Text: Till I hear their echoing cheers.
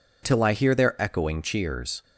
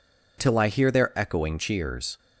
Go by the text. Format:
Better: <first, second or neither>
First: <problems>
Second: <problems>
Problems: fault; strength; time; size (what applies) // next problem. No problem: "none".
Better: neither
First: none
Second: none